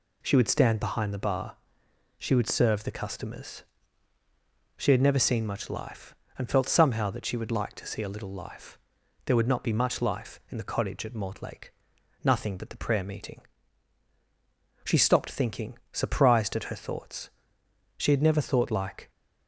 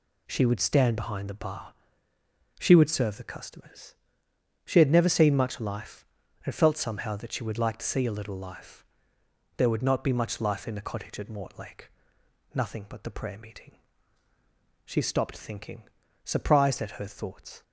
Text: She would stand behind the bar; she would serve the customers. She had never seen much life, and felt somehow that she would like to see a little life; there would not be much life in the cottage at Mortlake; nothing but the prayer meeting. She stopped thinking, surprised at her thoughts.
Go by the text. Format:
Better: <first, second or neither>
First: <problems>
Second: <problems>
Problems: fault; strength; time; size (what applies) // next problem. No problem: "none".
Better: second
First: goes on to say "She had never thought like"; noticeable; from 17.9 s on; 1.1 s long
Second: none